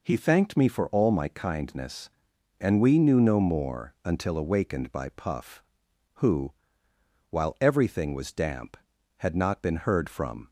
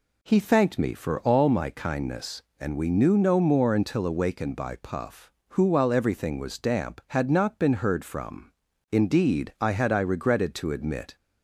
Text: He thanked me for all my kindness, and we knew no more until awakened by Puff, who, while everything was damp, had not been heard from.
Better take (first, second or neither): first